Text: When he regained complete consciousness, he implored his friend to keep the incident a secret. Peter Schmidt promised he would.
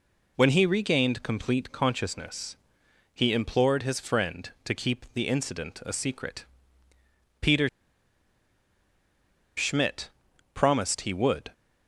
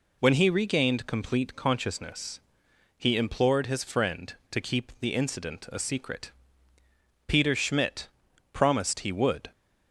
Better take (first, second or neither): second